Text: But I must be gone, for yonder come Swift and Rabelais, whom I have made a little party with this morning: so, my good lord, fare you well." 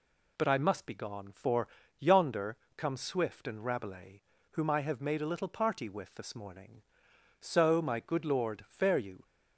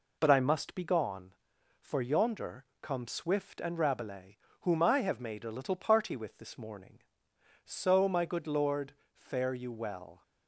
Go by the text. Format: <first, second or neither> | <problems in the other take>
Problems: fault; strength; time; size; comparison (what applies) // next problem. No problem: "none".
second | pauses between "for" and "yonder"; slight; at 1.6 s; 0.32 s long // pauses between "yonder" and "come"; slight; at 2.5 s; 0.20 s long; slight in the second // stops before "well"; at 9.2 s